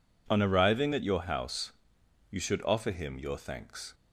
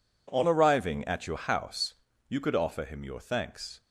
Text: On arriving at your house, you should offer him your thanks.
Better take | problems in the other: first | says "could" for "should"; at 2.4 s

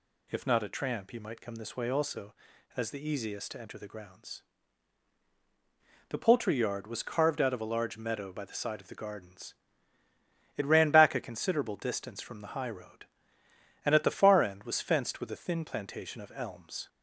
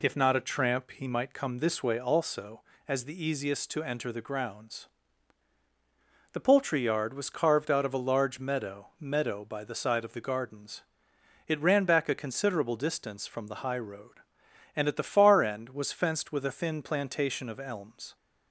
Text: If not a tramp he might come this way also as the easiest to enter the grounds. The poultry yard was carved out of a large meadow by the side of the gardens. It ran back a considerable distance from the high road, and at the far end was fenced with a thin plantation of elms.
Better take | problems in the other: first | says "meadow" twice; at 8.9 s

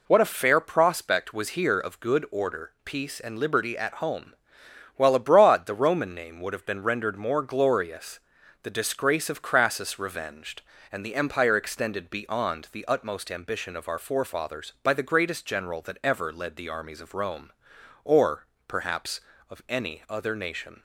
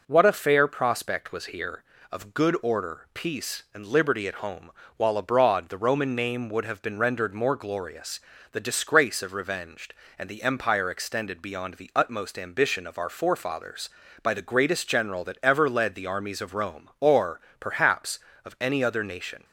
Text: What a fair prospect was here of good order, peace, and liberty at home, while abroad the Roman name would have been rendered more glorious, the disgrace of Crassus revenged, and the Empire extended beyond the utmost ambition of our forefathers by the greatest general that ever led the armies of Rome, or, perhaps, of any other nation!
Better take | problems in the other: first | skips "Crassus"; at 9.3 s

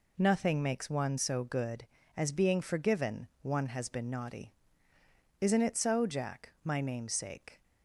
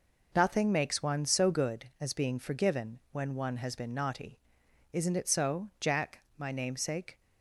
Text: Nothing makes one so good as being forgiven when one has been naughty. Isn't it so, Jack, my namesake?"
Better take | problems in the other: second | skips "when"; at 3.3 s

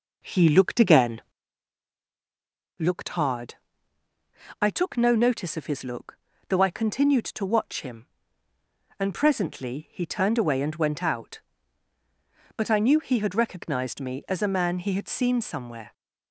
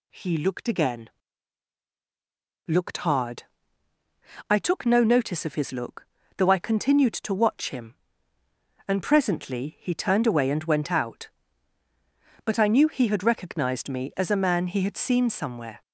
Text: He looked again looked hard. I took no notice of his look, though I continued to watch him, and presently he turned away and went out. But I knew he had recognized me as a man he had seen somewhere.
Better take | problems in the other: second | starts louder than the rest; noticeable; until 1.4 s; 4.5 dB // pauses between "again" and "looked"; strong; at 1.2 s; 1.5 s long; strong in the second

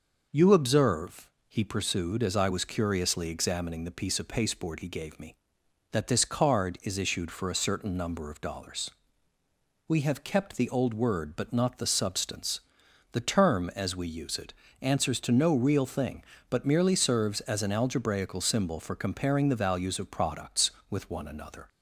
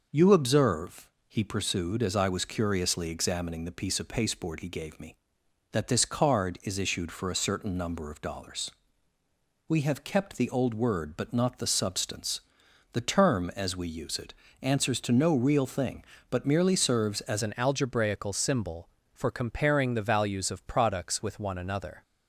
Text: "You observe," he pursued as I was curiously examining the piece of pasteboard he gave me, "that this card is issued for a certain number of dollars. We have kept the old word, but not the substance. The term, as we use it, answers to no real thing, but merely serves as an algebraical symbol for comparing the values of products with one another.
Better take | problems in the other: first | changes voice at "an"; from 17.4 s on; 4.6 s long

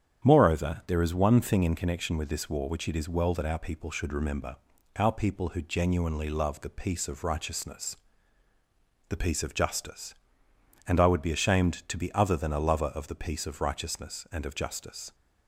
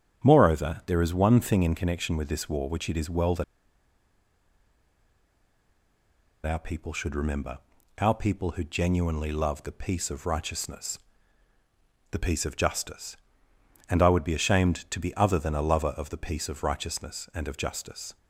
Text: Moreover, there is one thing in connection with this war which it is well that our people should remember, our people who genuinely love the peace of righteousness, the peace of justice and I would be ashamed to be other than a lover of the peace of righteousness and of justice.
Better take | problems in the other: first | starts louder than the rest; strong; until 1.3 s; 9 dB; strong in the first // pauses between "that" and "our"; strong; at 3.4 s; 3.0 s long

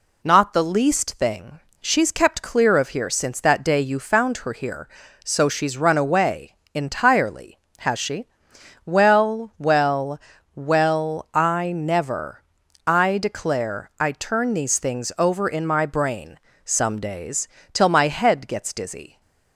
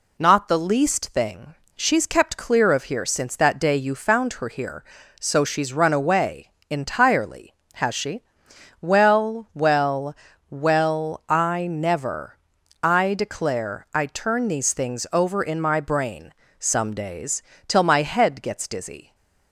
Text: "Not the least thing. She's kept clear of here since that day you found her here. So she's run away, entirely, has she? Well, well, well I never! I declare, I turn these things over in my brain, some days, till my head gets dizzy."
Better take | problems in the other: neither | none

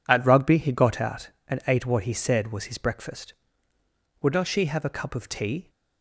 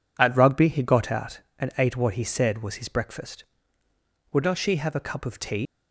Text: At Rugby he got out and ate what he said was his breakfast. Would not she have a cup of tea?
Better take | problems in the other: first | leaves "tea" unfinished; at 5.6 s; 145 ms

